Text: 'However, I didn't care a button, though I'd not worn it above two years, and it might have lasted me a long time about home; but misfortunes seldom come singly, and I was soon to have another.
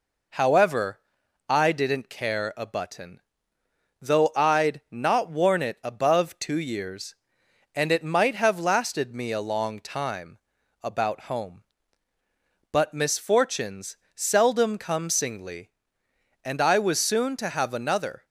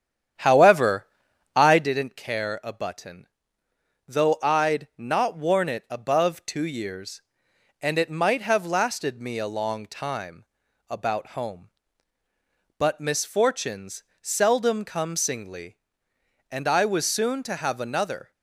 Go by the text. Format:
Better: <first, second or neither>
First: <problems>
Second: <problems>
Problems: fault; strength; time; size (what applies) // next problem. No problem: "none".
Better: first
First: pauses between "time" and "about"; at 10.3 s; 0.44 s long // pauses between "misfortunes" and "seldom"; slight; at 13.9 s; 0.22 s long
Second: starts louder than the rest; strong; until 1.9 s; 9.5 dB // pauses between "time" and "about"; at 10.4 s; 0.44 s long // pauses between "misfortunes" and "seldom"; slight; at 14.0 s; 0.22 s long